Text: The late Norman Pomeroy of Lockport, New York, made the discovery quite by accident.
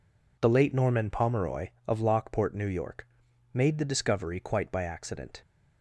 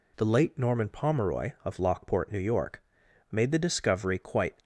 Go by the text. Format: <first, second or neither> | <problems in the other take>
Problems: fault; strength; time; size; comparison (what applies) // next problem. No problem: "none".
first | stops before "by accident"; at 4.6 s